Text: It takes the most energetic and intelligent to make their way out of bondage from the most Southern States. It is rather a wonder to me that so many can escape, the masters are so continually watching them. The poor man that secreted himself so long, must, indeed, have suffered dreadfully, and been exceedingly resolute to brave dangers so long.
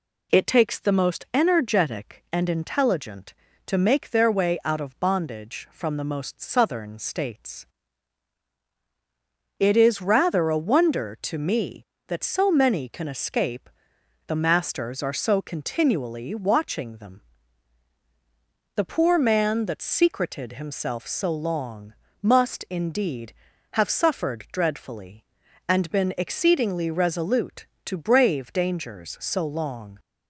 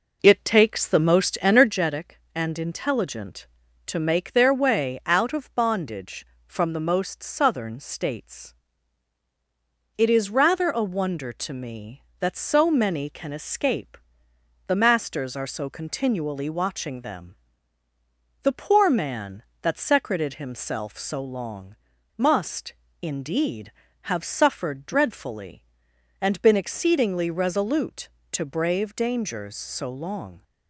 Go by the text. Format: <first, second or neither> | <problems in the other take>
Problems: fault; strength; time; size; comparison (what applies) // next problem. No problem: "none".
first | starts louder than the rest; noticeable; until 1.9 s; 4.5 dB